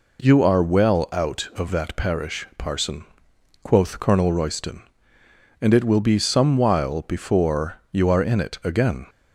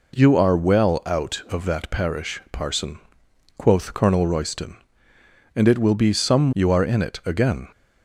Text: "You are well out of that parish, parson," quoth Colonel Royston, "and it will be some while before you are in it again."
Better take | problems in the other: first | skips "while before"; at 6.5 s

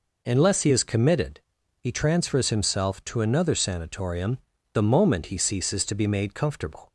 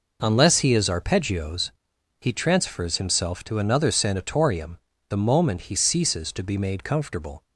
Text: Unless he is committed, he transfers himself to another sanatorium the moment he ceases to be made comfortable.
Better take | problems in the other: first | says "arpeggios" for "committed"; at 0.8 s // pauses between "sanatorium" and "the"; slight; at 4.7 s; 0.31 s long; also in the first

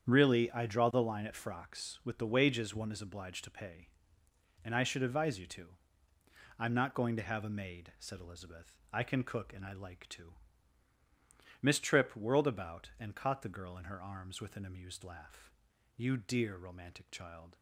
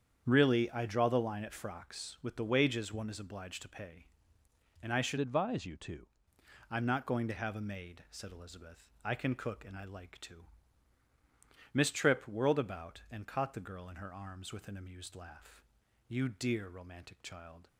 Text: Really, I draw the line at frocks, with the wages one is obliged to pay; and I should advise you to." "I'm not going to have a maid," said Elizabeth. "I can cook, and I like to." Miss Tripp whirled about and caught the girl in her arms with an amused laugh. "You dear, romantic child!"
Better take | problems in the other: first | starts louder than the rest; strong; until 1.2 s; 8 dB; strong in the first // changes voice from "advise" to "to"; from 5.1 to 6.0 s; 0.9 s long

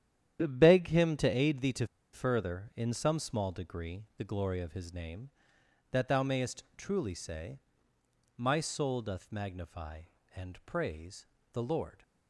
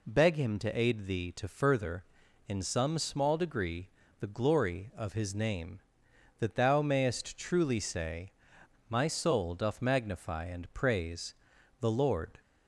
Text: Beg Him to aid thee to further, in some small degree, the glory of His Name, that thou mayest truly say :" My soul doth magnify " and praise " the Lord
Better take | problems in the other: second | starts louder than the rest; strong; until 1.4 s; 10 dB // pauses between "to" and "further"; slight; at 1.8 s; 0.28 s long

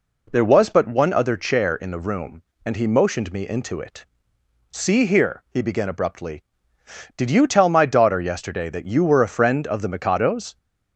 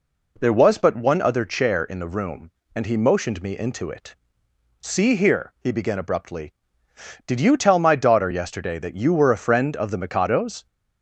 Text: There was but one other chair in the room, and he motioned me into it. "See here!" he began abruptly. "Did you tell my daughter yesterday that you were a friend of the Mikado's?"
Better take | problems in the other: neither | none

